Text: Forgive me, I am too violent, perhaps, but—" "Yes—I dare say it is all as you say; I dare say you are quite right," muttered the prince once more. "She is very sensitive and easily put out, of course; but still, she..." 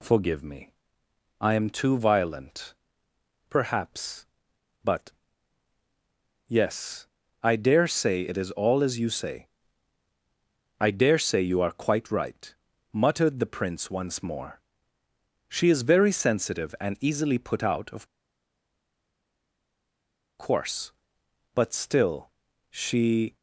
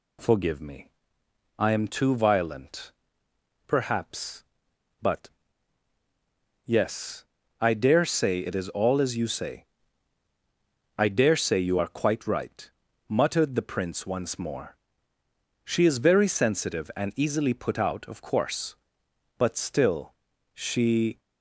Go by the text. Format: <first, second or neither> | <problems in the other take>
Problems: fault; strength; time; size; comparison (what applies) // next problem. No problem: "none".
second | pauses between "of" and "course"; strong; at 18.0 s; 2.3 s long